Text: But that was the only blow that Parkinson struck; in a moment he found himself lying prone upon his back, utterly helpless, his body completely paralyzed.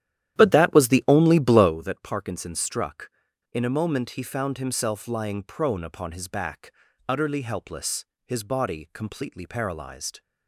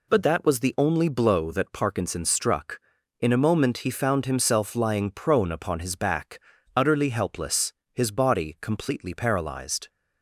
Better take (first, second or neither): second